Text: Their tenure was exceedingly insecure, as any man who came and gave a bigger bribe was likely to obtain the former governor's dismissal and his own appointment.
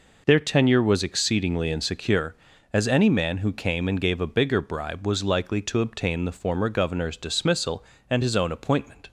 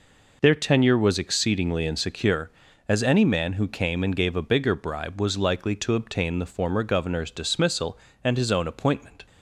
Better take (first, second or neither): neither